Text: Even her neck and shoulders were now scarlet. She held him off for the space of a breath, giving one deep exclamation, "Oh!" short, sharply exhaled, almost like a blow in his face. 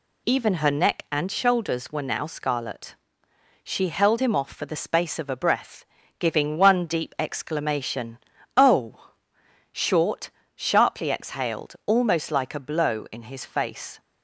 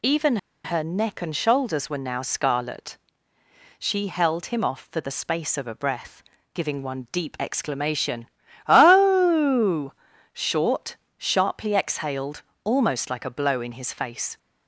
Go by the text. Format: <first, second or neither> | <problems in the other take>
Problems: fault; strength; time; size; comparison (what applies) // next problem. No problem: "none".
first | pauses between "Even" and "her"; slight; at 0.3 s; 0.27 s long